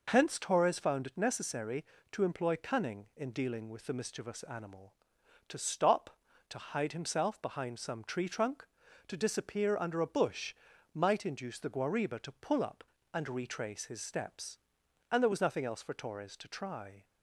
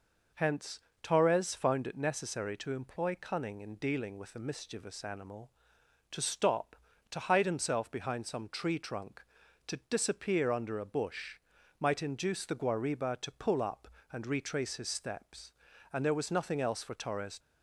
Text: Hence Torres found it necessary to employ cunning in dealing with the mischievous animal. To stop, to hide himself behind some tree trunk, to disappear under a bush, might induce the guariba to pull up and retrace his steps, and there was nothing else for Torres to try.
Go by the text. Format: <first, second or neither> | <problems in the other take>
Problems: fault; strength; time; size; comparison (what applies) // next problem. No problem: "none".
first | pauses between "Hence" and "Torres"; slight; at 0.7 s; 0.24 s long // stops before "to try"; at 17.3 s